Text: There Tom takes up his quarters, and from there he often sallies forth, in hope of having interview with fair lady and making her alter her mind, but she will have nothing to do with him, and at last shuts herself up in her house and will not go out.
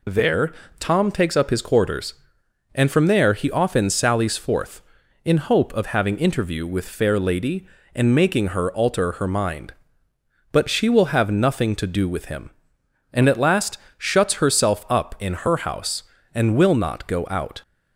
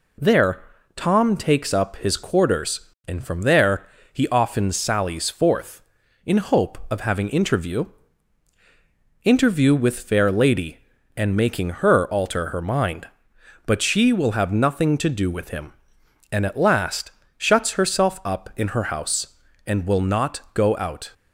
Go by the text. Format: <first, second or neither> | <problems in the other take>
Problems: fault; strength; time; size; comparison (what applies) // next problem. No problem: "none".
first | pauses between "There" and "Tom"; slight; at 0.6 s; 0.34 s long; slight in the first // pauses between "there" and "he"; slight; at 3.8 s; 0.24 s long // says "interview" twice; at 9.2 s // pauses between "last" and "shuts"; slight; at 17.1 s; 0.26 s long; slight in the first